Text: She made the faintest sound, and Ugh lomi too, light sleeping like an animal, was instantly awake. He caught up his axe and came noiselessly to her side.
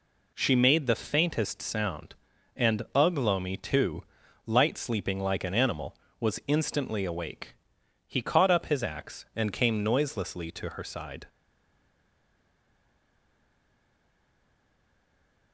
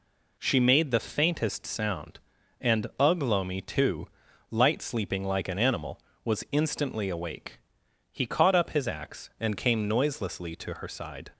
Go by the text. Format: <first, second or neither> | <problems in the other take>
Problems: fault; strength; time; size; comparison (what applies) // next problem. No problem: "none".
second | stays silent after the last word; strong; from 11.2 s on; 4.3 s long